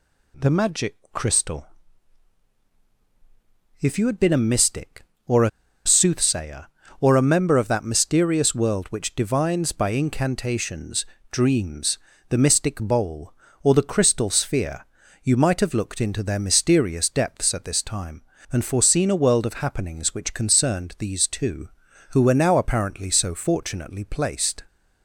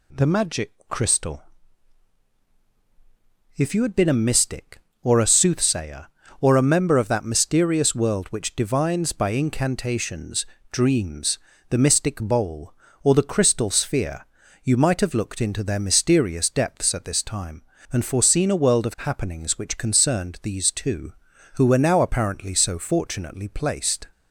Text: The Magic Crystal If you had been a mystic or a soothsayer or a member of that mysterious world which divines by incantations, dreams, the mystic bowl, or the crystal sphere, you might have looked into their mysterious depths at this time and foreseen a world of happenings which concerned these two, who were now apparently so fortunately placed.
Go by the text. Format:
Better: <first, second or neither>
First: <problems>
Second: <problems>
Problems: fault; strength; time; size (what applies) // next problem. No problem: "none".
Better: second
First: pauses between "Magic" and "Crystal"; slight; at 0.9 s; 0.16 s long // pauses between "Crystal" and "If"; strong; at 1.6 s; 2.1 s long // pauses between "a" and "soothsayer"; at 5.4 s; 0.37 s long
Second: pauses between "Magic" and "Crystal"; slight; at 0.7 s; 0.16 s long // pauses between "Crystal" and "If"; strong; at 1.4 s; 2.1 s long